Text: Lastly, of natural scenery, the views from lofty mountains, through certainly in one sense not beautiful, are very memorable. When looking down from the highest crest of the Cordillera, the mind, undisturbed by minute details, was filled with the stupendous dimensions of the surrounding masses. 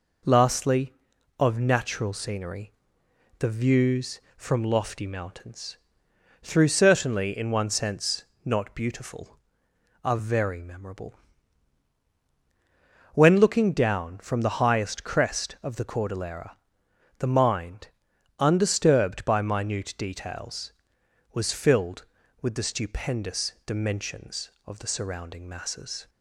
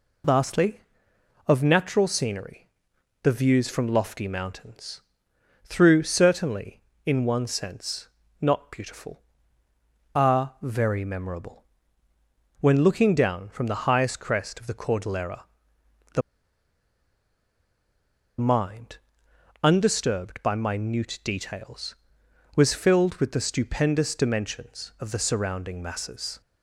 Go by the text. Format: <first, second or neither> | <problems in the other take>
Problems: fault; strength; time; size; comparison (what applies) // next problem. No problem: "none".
first | pauses between "sense" and "not"; slight; at 8.0 s; 0.34 s long; slight in the first // pauses between "the" and "mind"; strong; at 16.2 s; 2.1 s long